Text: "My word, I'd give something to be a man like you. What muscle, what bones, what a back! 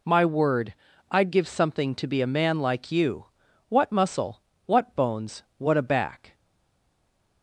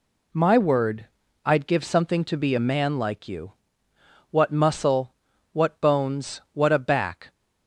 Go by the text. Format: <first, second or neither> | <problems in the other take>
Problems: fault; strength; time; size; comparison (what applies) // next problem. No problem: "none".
second | stays silent after the last word; from 6.3 s on; 1.1 s long